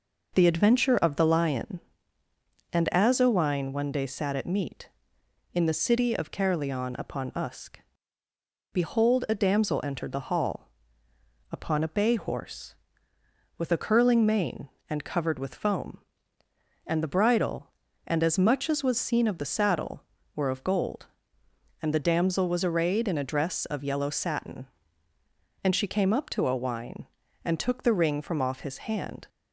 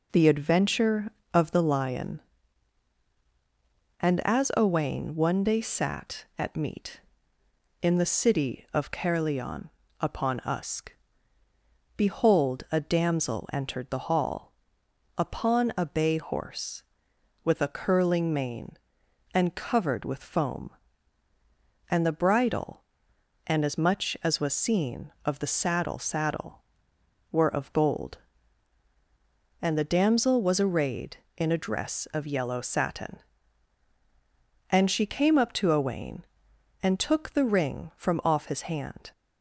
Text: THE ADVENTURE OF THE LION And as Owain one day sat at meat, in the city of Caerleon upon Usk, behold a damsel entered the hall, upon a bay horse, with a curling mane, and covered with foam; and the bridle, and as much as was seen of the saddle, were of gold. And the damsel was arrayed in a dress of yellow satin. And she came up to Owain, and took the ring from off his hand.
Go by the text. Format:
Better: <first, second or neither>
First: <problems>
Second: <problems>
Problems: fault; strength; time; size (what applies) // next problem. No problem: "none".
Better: first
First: none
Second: pauses between "Caerleon" and "upon"; slight; at 9.6 s; 0.30 s long // says "saddle" twice; at 25.9 s